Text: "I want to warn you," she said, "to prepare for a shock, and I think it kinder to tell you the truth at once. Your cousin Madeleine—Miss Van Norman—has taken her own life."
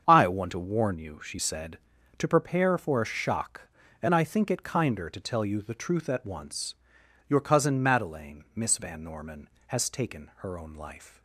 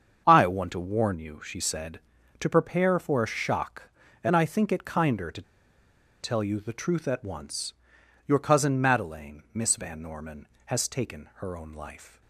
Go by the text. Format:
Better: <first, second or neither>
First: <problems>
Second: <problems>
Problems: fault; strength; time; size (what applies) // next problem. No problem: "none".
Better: first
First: starts louder than the rest; strong; until 1.0 s; 7 dB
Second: starts louder than the rest; strong; until 1.2 s; 7 dB // pauses between "to" and "tell"; noticeable; at 5.4 s; 0.79 s long